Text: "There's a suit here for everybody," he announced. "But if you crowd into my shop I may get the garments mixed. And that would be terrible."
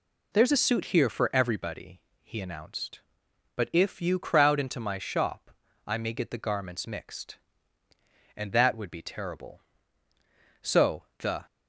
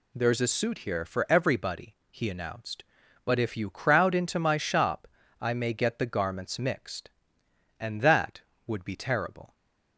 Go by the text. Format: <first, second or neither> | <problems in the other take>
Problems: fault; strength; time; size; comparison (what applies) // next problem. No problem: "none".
second | pauses between "shop" and "I"; slight; at 5.4 s; 0.36 s long; slight in the second // goes on to say "So the"; noticeable; from 10.6 s on; 0.84 s long